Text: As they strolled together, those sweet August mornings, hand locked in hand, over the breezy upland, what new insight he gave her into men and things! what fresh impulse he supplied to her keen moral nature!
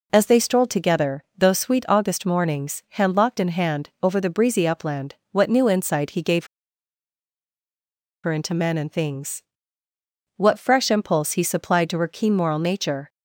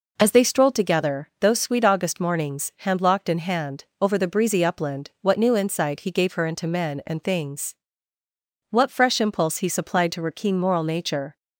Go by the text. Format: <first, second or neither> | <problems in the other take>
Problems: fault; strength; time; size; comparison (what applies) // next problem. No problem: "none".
second | pauses between "gave" and "her"; strong; at 6.4 s; 1.7 s long